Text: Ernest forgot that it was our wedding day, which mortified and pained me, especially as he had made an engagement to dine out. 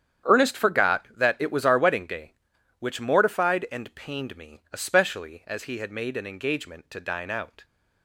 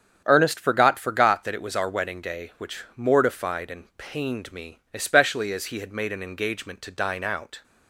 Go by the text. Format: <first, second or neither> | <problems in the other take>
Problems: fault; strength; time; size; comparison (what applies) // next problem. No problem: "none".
first | starts louder than the rest; strong; until 1.2 s; 8 dB; strong in the first // says "forgot" twice; at 0.9 s